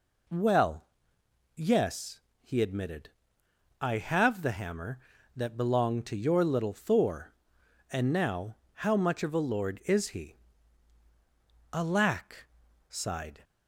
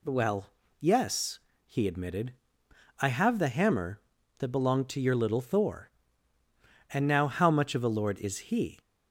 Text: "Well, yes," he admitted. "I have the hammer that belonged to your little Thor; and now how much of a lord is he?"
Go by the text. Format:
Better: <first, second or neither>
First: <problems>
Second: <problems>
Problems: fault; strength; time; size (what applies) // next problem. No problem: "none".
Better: second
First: pauses between "now" and "how"; slight; at 8.5 s; 0.17 s long // goes on to say "Alack sighed"; strong; from 11.7 s on; 1.7 s long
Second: none